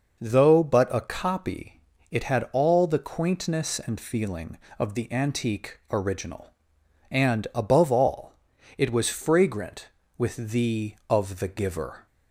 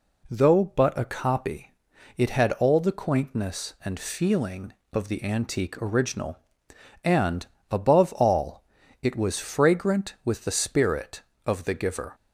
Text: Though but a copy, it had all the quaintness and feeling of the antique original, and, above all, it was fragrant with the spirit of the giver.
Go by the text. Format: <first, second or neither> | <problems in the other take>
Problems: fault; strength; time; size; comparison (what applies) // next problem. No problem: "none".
second | skips "spirit"; at 11.0 s